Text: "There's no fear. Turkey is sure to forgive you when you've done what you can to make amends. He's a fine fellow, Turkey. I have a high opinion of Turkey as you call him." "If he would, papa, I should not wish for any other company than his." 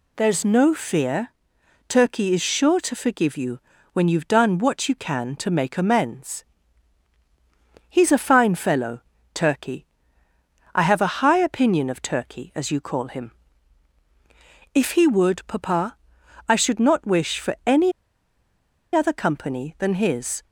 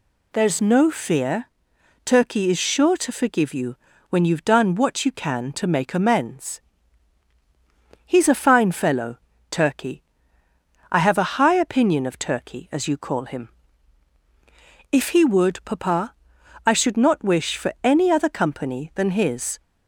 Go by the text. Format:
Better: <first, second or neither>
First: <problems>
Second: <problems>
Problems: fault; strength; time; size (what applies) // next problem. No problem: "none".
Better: second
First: pauses between "you" and "when"; slight; at 3.5 s; 0.34 s long // pauses between "any" and "other"; at 17.9 s; 1.0 s long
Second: pauses between "you" and "when"; slight; at 3.7 s; 0.34 s long